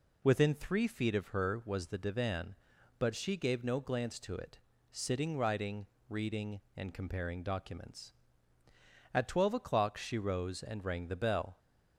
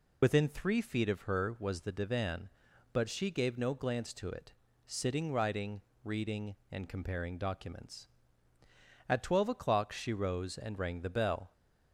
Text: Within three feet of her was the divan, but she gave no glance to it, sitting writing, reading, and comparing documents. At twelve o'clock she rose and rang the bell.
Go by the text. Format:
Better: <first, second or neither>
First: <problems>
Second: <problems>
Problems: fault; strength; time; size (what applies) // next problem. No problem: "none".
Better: first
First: none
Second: loses the start of "Within"; at 0.2 s; 70 ms